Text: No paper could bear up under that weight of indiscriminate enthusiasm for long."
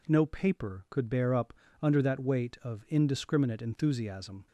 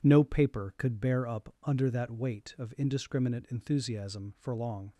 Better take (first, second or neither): second